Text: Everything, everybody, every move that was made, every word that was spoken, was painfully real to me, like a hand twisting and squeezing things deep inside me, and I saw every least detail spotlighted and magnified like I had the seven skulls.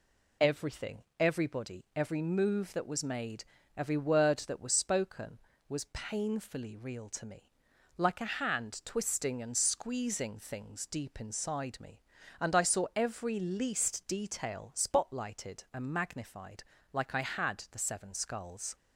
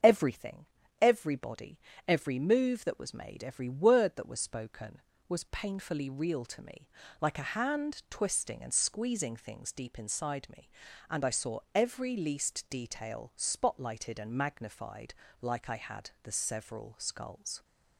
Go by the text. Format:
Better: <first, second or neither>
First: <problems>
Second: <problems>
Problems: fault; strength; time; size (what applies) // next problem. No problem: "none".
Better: first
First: pauses between "magnified" and "like"; slight; at 16.6 s; 0.28 s long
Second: starts louder than the rest; until 1.3 s; 7 dB // pauses between "saw" and "every"; slight; at 11.5 s; 0.16 s long // pauses between "magnified" and "like"; slight; at 15.1 s; 0.28 s long // says "several" for "seven"; at 16.3 s